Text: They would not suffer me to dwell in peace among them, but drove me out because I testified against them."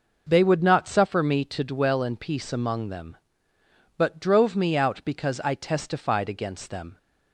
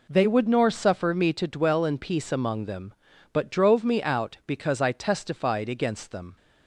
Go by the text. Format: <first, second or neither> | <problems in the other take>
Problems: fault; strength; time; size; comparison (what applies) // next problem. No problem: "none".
first | says "nor" for "not"; at 0.4 s